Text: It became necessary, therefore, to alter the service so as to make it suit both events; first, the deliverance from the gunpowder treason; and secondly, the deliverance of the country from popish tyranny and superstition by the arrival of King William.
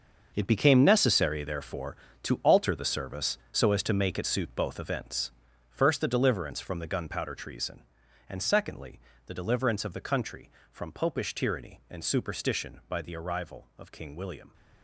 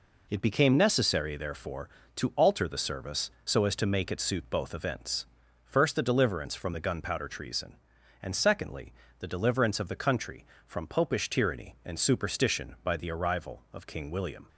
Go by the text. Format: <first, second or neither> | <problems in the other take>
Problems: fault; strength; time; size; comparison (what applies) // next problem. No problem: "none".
second | gets quieter; strong; throughout; 13 dB